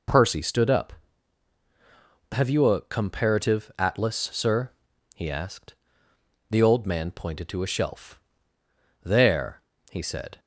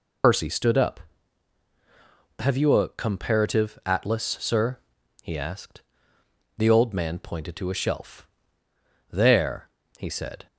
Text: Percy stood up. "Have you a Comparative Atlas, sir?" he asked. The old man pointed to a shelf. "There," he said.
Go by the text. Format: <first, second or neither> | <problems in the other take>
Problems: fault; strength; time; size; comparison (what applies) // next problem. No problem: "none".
first | loses the start of "Percy"; at 0.2 s; 90 ms